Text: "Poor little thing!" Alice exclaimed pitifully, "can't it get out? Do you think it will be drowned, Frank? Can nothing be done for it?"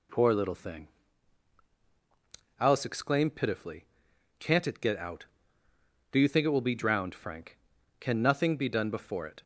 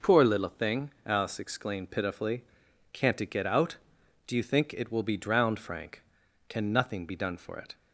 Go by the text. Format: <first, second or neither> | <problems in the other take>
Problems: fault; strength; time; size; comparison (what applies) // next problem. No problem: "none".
second | says "before" for "for"; at 8.9 s